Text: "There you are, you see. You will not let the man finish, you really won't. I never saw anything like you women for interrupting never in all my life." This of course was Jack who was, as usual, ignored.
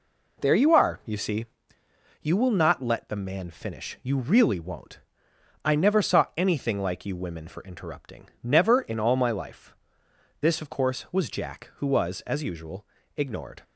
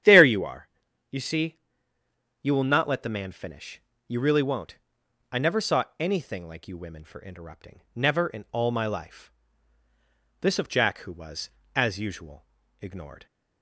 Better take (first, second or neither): first